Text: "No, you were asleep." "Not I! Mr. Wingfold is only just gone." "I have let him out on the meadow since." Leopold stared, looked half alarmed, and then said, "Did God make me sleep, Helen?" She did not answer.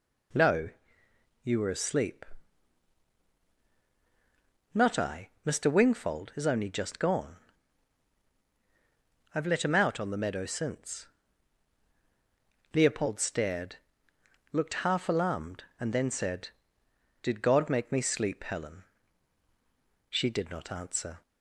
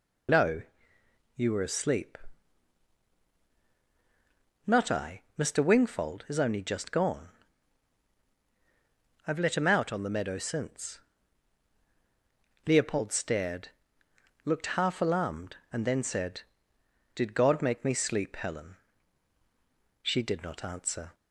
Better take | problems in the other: first | loses the start of "No"; at 0.2 s; 55 ms

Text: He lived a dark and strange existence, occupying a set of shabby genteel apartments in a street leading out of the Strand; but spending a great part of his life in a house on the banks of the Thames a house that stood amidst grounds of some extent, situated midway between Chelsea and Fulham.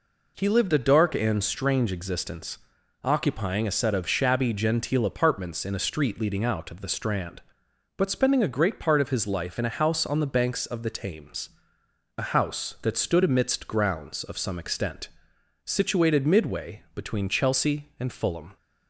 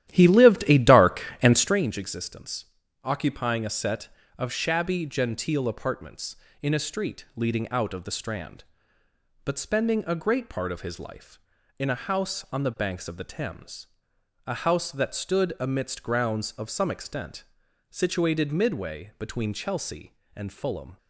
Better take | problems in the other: first | starts louder than the rest; strong; until 1.9 s; 12.5 dB // pauses between "Thames" and "a"; noticeable; at 13.8 s; 0.58 s long; noticeable in the first

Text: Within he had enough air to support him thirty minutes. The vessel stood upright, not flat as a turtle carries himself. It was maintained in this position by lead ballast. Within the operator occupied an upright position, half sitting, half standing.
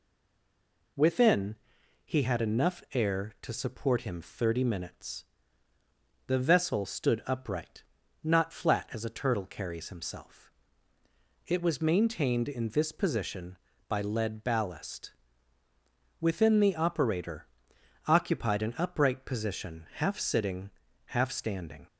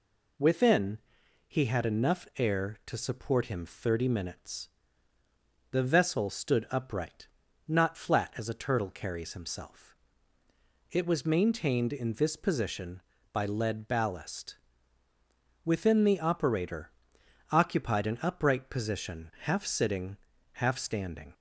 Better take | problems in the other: second | stays silent before the first word; slight; until 0.9 s; 0.9 s long // pauses between "Within" and "he"; noticeable; at 1.5 s; 0.48 s long; noticeable in the second // pauses between "operator" and "occupied"; noticeable; at 17.4 s; 0.60 s long; noticeable in the second

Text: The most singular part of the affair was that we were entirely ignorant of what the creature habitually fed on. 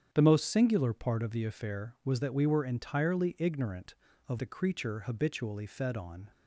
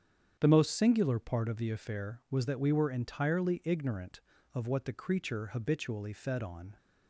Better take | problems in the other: second | starts louder than the rest; strong; until 1.1 s; 8.5 dB; strong in the second // skips "what"; at 4.3 s

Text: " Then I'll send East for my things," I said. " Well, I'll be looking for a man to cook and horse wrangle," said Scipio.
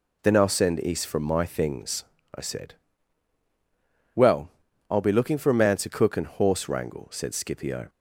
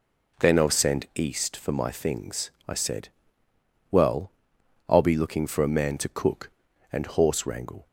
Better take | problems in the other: first | stops before "said Scipio"; at 7.8 s

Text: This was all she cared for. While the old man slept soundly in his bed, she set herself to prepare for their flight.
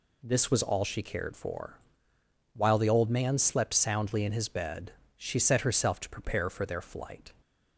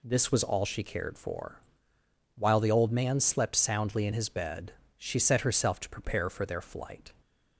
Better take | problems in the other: neither | none

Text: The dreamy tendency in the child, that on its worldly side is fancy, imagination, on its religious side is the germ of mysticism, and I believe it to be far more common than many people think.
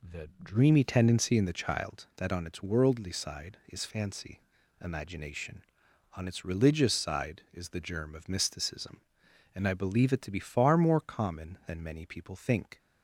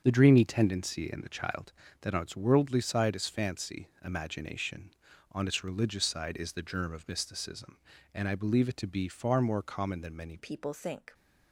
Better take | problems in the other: first | starts louder than the rest; until 1.0 s; 7 dB // changes voice at "people"; from 10.3 s on; 0.8 s long

